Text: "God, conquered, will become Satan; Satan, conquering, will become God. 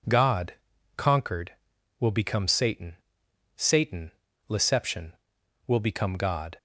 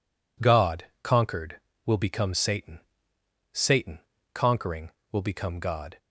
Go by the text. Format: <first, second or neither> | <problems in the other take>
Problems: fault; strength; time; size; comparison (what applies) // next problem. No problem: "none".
second | says "leception" for "conquering"; at 4.4 s